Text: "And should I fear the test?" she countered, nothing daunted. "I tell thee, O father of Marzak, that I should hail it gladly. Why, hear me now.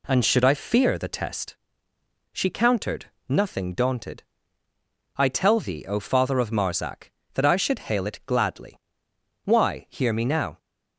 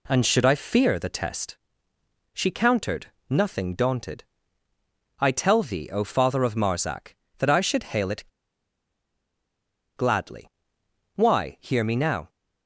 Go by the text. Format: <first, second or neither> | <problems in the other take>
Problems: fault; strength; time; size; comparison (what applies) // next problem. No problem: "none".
first | pauses between "it" and "gladly"; strong; at 8.2 s; 1.7 s long